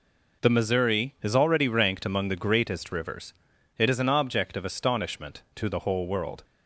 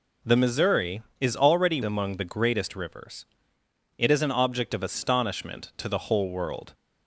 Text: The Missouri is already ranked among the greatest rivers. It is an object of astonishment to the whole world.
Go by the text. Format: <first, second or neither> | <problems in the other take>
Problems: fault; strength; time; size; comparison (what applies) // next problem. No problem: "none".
first | skips "ranked"; at 1.8 s